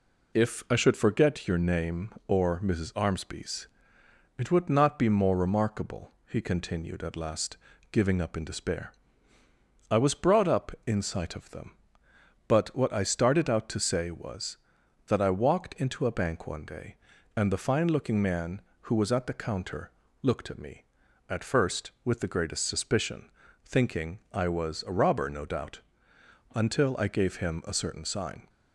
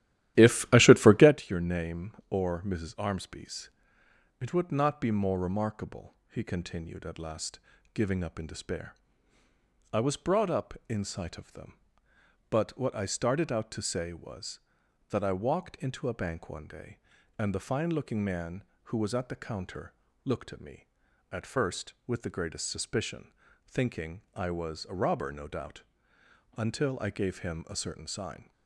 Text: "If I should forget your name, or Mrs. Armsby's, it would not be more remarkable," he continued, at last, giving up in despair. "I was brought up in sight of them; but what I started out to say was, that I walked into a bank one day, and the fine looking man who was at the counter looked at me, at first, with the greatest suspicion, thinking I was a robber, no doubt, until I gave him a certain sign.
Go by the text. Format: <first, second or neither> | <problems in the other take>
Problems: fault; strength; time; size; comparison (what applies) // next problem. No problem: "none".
first | starts louder than the rest; strong; until 1.4 s; 13.5 dB // pauses between "counter" and "looked"; slight; at 19.9 s; 0.32 s long; slight in the first